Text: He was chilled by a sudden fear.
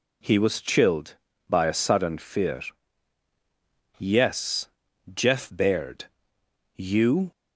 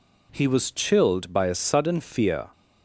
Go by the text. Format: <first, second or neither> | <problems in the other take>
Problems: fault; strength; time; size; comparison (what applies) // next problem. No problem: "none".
second | goes on to say "Yes Jeff Baird You"; strong; from 3.9 s on; 3.3 s long